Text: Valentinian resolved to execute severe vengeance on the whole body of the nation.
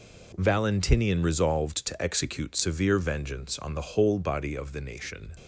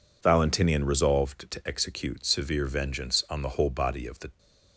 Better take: first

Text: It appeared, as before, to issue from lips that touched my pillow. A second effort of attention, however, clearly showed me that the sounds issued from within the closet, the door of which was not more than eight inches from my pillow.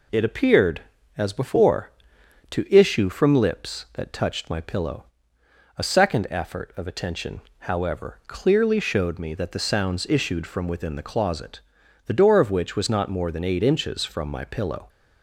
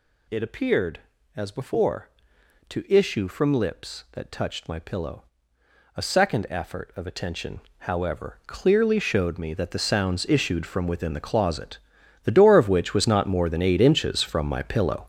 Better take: first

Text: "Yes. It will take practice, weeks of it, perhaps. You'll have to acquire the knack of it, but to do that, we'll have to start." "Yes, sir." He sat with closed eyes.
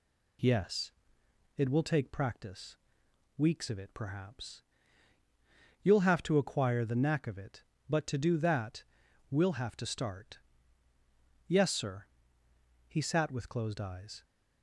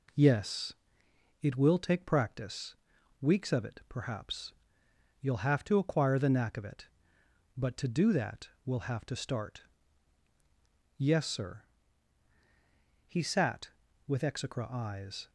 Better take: first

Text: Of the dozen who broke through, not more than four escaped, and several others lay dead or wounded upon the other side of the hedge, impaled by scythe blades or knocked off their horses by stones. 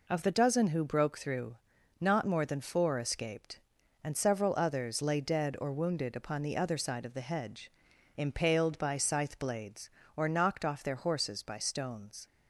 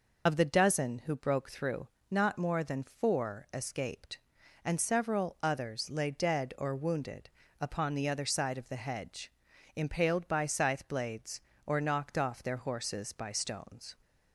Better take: first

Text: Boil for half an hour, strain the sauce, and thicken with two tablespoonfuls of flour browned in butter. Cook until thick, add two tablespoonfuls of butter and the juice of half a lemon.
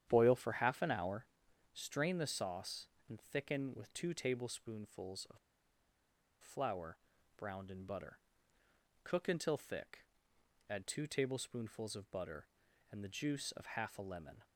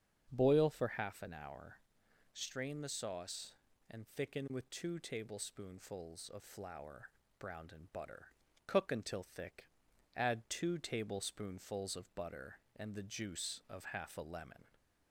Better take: second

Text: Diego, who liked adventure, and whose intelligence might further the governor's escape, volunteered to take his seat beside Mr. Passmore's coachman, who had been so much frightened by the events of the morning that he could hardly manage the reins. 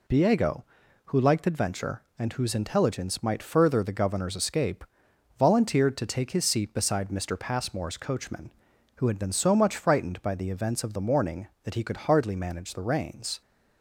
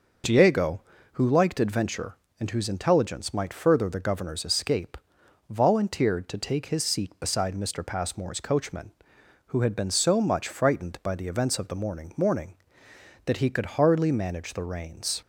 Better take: first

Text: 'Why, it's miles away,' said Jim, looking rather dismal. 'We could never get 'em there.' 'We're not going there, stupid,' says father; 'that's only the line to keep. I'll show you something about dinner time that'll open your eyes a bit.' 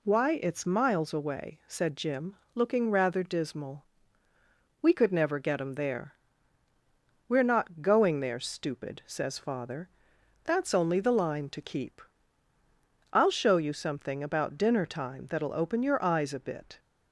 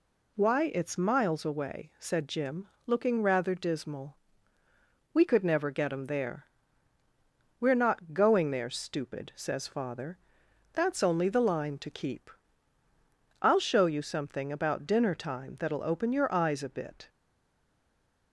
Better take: first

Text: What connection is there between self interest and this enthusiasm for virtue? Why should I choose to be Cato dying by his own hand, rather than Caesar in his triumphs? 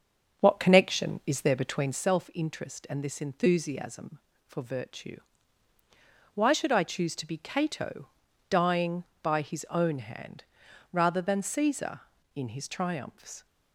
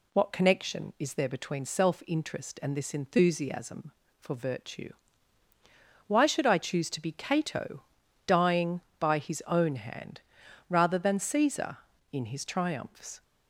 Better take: second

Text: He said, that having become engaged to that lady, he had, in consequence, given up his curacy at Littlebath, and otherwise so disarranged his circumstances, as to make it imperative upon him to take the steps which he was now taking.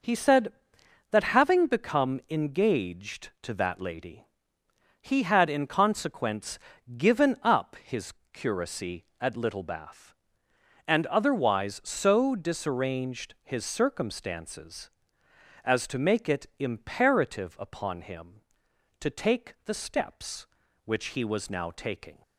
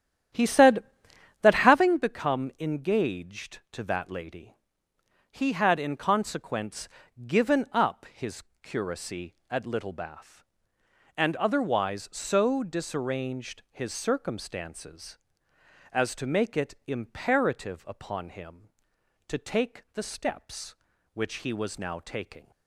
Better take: first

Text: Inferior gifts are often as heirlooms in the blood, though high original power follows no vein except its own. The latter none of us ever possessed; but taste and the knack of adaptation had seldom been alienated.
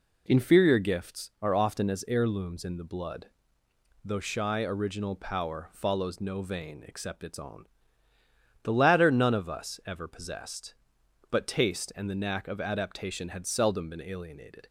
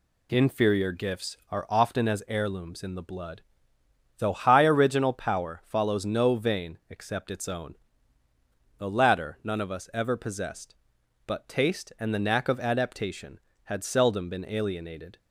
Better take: second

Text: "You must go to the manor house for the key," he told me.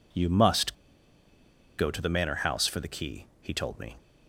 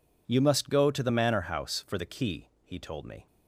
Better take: second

